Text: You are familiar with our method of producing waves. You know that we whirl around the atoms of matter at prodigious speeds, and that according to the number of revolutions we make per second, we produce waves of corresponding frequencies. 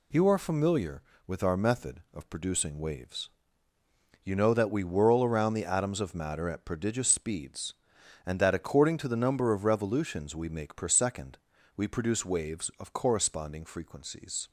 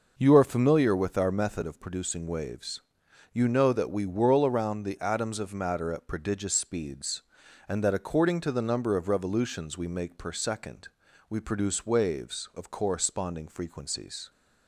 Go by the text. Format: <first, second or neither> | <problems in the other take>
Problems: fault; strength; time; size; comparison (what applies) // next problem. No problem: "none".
neither | none